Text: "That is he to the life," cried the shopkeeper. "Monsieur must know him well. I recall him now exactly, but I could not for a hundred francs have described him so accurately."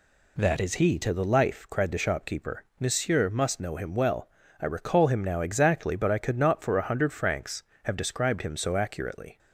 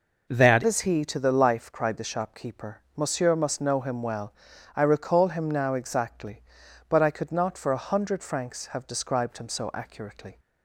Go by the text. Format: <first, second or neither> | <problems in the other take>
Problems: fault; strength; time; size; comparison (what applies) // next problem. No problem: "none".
first | changes voice at "is"; from 0.6 s on; 9.7 s long